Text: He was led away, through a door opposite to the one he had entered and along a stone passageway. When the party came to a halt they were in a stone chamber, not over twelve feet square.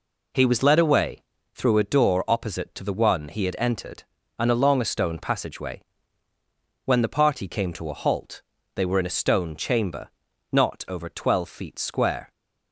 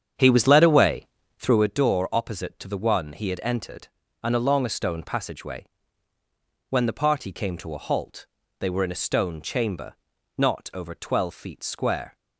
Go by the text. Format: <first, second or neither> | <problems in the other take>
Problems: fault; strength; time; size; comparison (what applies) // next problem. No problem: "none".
first | starts louder than the rest; strong; until 1.7 s; 8 dB // pauses between "halt" and "they"; slight; at 8.2 s; 0.32 s long; slight in the first